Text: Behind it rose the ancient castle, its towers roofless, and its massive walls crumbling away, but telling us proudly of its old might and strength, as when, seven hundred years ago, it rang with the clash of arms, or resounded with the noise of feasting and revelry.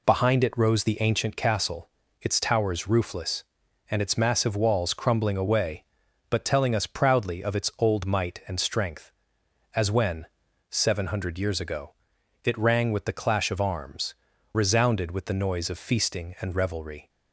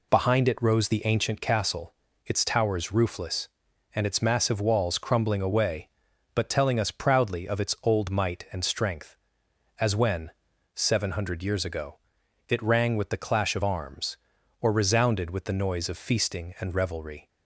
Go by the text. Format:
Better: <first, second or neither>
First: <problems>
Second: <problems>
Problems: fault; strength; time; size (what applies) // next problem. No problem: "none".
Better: second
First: skips "or"; at 14.3 s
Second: none